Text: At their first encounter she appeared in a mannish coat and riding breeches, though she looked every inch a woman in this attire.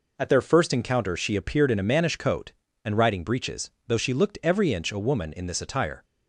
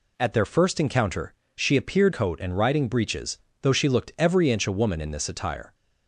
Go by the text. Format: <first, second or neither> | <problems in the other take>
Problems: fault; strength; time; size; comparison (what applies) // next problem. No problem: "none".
first | pauses between "encounter" and "she"; slight; at 1.3 s; 0.24 s long // skips "in a mannish"; at 2.1 s